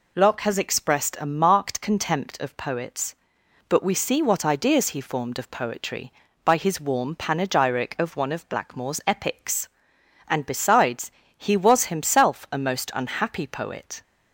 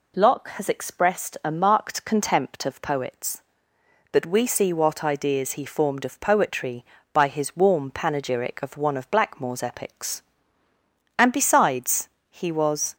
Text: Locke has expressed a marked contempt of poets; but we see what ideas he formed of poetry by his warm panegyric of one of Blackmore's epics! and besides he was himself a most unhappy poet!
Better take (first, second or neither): first